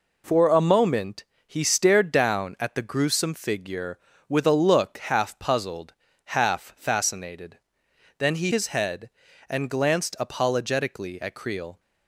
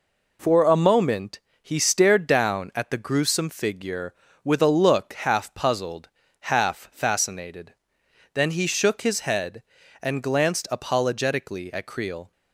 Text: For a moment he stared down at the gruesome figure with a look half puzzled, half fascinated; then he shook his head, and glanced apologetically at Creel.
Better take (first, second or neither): second